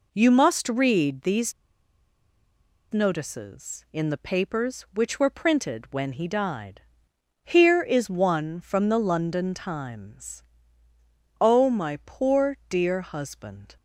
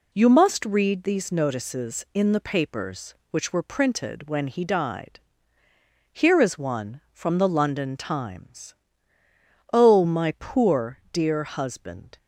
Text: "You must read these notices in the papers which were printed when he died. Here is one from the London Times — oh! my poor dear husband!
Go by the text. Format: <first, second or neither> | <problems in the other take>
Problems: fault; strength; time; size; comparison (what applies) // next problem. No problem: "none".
second | pauses between "these" and "notices"; strong; at 1.5 s; 1.3 s long